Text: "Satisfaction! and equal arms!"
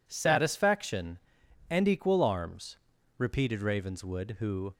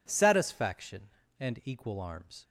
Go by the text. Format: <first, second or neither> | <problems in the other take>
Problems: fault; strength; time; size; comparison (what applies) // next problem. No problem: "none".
second | goes on to say "repeated Ravenswood who"; from 3.1 s on; 1.5 s long